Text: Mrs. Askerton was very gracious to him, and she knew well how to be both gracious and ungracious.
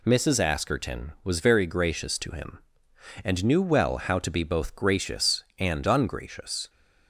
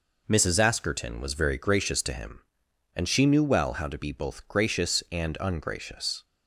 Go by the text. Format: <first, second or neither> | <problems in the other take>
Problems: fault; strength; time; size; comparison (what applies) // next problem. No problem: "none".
second | skips "she"; at 3.4 s